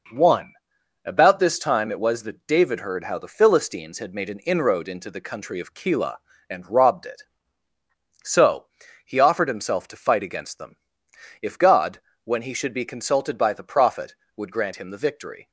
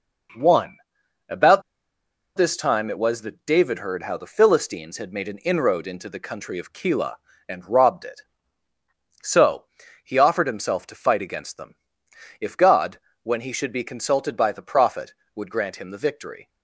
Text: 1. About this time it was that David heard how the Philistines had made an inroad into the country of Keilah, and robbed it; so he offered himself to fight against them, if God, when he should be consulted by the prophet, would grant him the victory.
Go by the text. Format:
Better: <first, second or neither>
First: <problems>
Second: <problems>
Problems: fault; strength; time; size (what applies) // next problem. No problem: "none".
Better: first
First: pauses between "so" and "he"; slight; at 8.6 s; 0.36 s long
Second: pauses between "About" and "this"; noticeable; at 1.6 s; 0.76 s long // pauses between "so" and "he"; slight; at 9.6 s; 0.36 s long